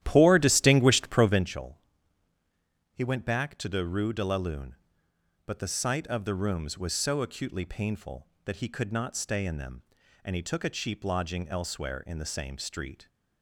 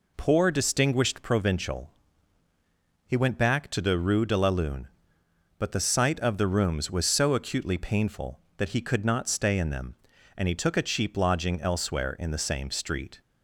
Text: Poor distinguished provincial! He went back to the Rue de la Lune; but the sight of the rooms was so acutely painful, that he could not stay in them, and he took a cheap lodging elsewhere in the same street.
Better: second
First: starts louder than the rest; strong; until 1.5 s; 12.5 dB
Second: none

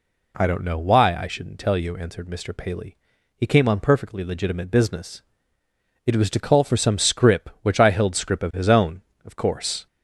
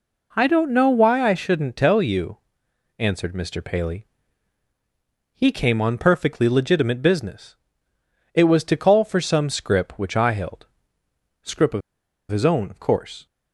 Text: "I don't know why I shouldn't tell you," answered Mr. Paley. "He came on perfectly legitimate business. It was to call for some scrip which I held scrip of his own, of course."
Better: first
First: none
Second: pauses between "held" and "scrip"; noticeable; at 10.6 s; 0.74 s long // pauses between "of" and "his"; noticeable; at 11.8 s; 0.50 s long

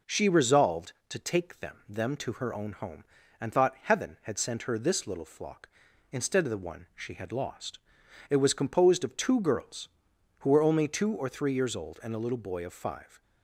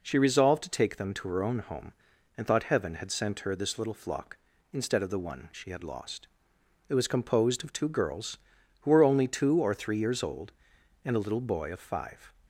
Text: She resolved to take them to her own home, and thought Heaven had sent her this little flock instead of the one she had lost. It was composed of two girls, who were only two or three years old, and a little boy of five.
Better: second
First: says "them" twice; at 1.8 s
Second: none

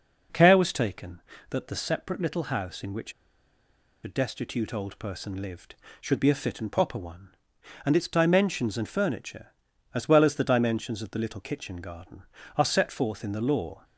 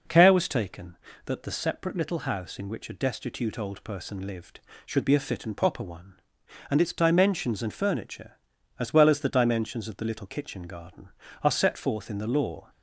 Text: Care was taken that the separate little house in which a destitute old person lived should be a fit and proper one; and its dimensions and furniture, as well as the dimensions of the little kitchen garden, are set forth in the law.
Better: second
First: pauses between "which" and "a"; noticeable; at 3.1 s; 0.90 s long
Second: none

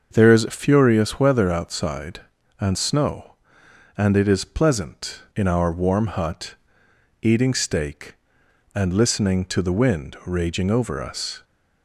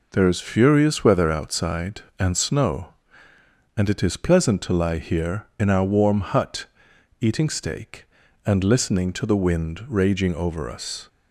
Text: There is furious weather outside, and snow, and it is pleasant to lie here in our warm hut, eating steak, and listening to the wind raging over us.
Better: second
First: starts louder than the rest; until 1.2 s; 6.5 dB // skips "to lie here"; at 5.2 s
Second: none

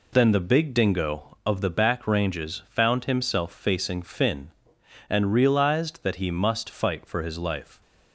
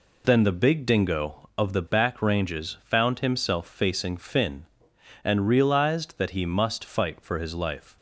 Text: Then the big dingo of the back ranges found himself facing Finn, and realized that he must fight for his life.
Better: neither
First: none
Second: none

